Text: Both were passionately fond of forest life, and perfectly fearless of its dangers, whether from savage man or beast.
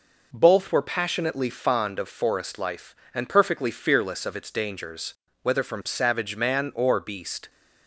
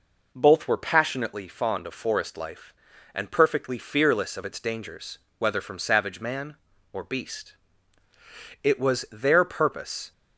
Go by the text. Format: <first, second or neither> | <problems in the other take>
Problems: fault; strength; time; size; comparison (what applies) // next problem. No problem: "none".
first | goes on to say "It was their purpose"; from 8.6 s on; 1.5 s long